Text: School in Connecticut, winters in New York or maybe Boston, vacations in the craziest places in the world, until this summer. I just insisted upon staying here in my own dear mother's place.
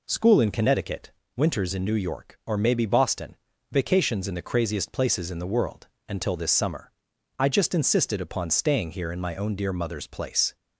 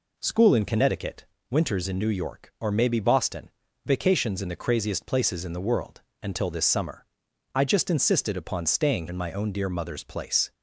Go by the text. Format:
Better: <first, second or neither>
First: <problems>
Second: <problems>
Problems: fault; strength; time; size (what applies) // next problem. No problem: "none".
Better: first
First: none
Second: skips "here"; at 9.0 s